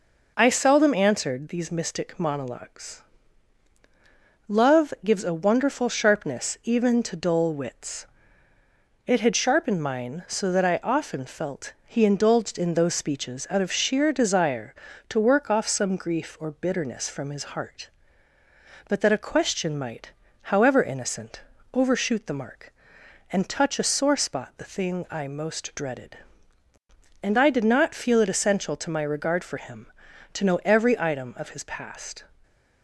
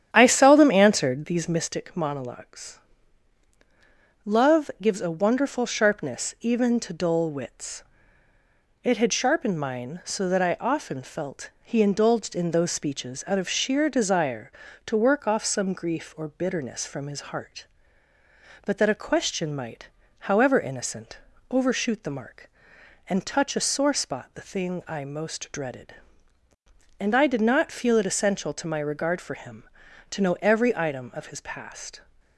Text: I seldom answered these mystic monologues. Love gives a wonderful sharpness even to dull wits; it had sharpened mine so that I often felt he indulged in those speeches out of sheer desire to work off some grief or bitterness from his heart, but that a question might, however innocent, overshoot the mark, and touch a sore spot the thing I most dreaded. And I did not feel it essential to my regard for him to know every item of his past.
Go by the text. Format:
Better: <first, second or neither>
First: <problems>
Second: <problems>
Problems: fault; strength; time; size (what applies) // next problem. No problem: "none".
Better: first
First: none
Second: starts louder than the rest; strong; until 1.8 s; 9.5 dB